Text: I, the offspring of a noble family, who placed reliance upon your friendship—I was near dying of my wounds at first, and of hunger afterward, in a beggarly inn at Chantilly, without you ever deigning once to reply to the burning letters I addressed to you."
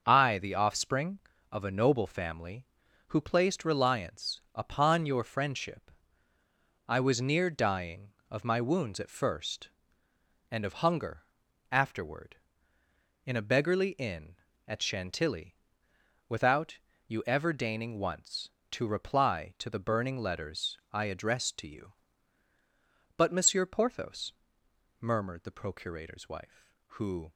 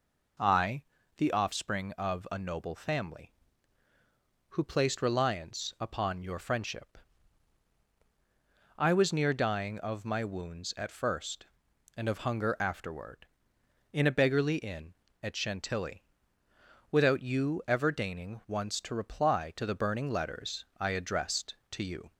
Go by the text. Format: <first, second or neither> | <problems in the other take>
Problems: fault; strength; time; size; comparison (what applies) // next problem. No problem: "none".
second | starts louder than the rest; until 1.0 s; 6.5 dB // pauses between "hunger" and "afterward"; noticeable; at 11.2 s; 0.48 s long // pauses between "without" and "you"; slight; at 16.7 s; 0.28 s long // goes on to say "But Monsieur Porthos murmured the procurator's wife who"; strong; from 23.1 s on; 4.1 s long